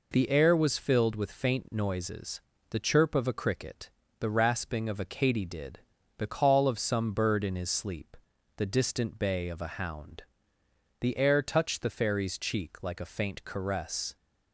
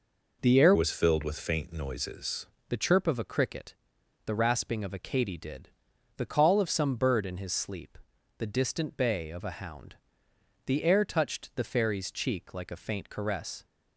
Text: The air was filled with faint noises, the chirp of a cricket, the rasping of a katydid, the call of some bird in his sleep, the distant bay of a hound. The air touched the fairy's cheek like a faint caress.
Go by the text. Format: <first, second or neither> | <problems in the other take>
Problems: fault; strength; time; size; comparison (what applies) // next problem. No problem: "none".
first | changes voice from "was" to "noises"; from 0.7 to 2.4 s; 1.7 s long